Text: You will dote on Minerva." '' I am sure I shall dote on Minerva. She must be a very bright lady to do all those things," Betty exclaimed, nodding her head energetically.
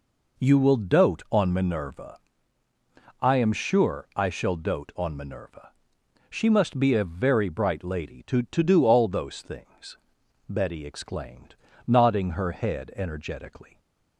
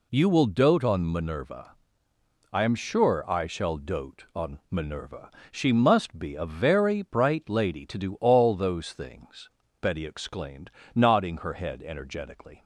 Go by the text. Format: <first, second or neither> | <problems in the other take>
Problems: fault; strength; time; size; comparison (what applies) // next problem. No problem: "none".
second | says "to" twice; at 8.4 s